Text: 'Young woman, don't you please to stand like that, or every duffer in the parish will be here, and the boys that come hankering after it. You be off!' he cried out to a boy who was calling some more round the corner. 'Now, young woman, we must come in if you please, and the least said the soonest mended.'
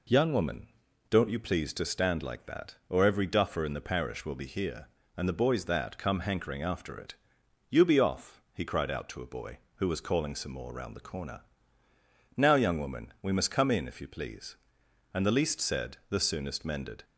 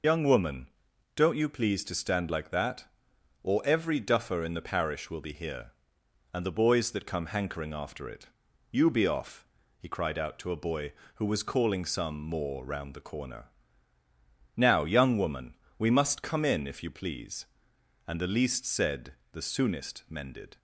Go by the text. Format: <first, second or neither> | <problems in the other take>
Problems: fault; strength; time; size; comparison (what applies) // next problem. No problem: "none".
first | loses the start of "Young"; at 0.0 s; 65 ms // pauses between "said" and "the"; slight; at 19.1 s; 0.18 s long